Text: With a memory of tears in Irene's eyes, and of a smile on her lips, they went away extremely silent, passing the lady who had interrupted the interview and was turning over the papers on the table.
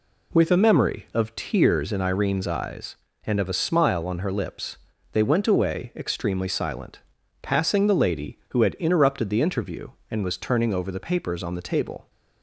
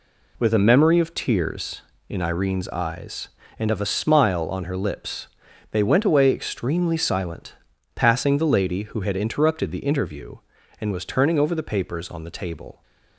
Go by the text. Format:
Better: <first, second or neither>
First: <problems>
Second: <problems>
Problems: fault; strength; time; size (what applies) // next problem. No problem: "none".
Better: neither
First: none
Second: none